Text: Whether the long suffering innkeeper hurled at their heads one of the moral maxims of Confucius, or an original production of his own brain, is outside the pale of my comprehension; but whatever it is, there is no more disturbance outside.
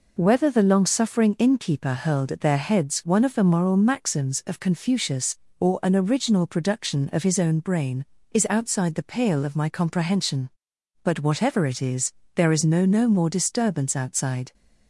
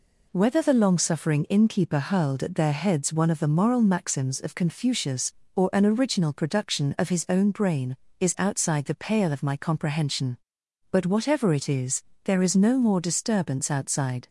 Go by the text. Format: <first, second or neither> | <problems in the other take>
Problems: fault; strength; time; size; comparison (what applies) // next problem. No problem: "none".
second | says "no" twice; at 12.8 s